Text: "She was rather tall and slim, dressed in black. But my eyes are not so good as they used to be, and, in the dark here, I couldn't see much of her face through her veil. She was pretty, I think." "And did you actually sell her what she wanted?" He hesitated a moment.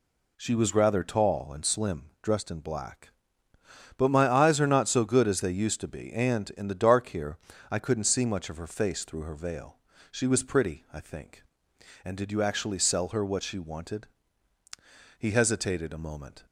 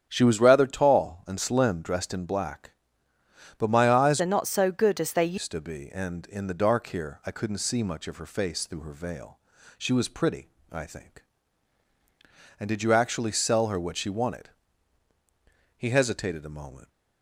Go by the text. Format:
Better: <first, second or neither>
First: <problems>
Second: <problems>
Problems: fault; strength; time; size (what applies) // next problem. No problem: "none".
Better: first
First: none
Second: starts louder than the rest; strong; until 1.0 s; 8.5 dB // changes voice from "are" to "they"; from 4.2 to 5.3 s; 1.1 s long